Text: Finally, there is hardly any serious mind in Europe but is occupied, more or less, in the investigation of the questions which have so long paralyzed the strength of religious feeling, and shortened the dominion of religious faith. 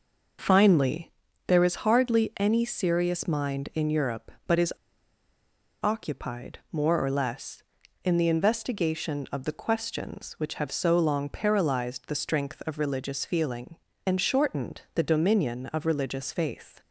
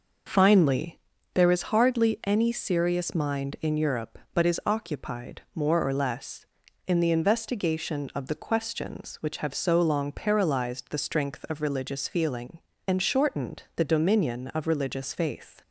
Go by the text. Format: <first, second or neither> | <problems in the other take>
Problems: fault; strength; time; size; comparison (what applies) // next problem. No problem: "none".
second | pauses between "is" and "occupied"; at 4.7 s; 1.1 s long